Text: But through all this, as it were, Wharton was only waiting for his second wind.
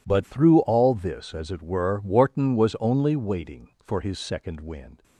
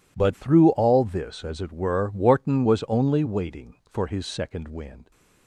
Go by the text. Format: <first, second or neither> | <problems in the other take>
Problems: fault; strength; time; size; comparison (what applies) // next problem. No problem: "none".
neither | none